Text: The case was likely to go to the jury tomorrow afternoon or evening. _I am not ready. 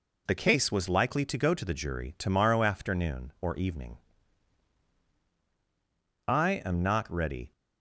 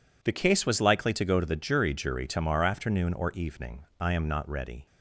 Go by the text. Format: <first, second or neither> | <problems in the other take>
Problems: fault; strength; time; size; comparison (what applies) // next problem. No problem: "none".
first | says "jury" twice; at 1.9 s